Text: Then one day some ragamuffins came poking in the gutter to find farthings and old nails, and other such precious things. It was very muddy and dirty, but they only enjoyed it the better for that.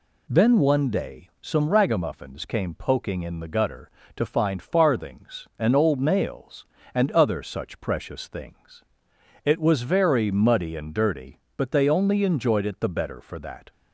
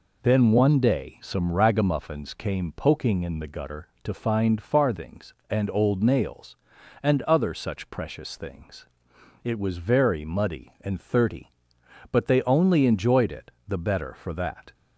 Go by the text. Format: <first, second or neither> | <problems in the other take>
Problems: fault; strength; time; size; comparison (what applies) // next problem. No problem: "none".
first | says "thirty" for "dirty"; at 10.9 s // pauses between "it" and "the"; slight; at 13.4 s; 0.16 s long